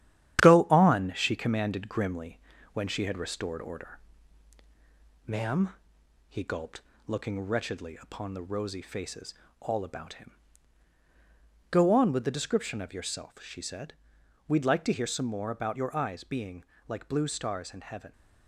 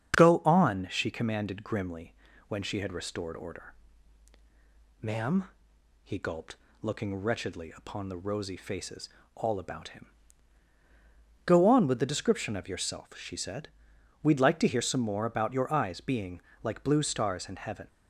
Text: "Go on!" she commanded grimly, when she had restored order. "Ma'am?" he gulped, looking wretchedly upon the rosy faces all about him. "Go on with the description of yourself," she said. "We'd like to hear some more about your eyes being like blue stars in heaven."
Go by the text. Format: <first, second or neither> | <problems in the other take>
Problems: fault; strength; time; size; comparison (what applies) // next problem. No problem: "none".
second | gets quieter; noticeable; throughout; 5.5 dB // starts louder than the rest; strong; until 1.5 s; 11 dB; strong in the second // pauses between "faces" and "all"; slight; at 9.3 s; 0.26 s long; slight in the second // pauses between "being" and "like"; slight; at 16.6 s; 0.22 s long; slight in the second